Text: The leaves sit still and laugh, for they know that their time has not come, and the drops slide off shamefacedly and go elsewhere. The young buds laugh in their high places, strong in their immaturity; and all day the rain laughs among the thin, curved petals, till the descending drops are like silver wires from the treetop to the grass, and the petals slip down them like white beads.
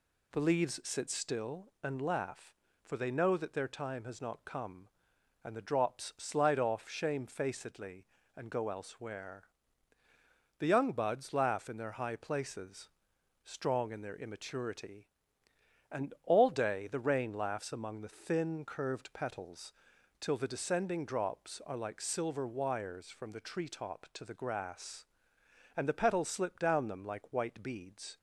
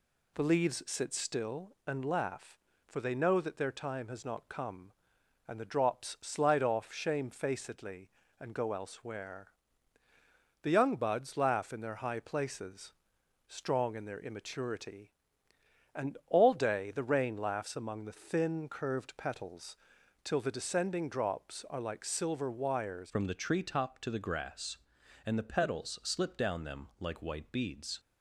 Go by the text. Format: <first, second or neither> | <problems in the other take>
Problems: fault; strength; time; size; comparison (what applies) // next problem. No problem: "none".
first | changes voice at "from"; from 23.0 s on; 4.9 s long